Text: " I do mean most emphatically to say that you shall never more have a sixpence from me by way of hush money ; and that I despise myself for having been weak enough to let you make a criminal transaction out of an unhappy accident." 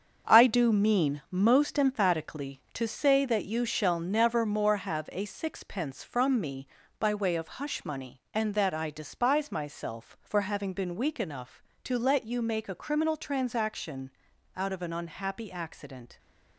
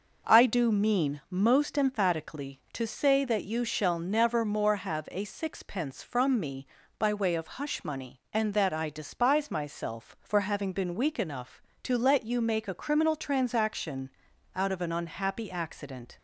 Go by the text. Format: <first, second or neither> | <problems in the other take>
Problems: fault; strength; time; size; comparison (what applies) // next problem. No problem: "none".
second | gets quieter; strong; throughout; 8 dB // pauses between "transaction" and "out"; noticeable; at 14.0 s; 0.46 s long; noticeable in the second